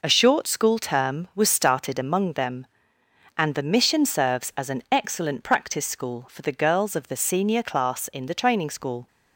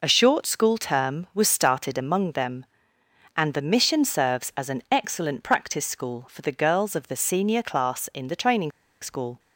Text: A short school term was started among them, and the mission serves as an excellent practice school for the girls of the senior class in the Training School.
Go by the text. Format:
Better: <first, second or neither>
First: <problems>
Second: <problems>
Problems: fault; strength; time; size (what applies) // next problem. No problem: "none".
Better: first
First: none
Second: pauses between "Training" and "School"; slight; at 8.7 s; 0.32 s long